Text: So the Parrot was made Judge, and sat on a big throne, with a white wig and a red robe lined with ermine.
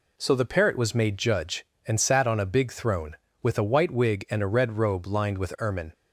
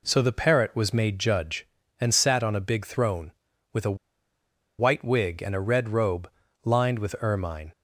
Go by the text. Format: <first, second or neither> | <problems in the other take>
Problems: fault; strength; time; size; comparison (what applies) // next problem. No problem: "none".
first | pauses between "a" and "white"; noticeable; at 3.9 s; 0.82 s long // pauses between "robe" and "lined"; slight; at 6.2 s; 0.34 s long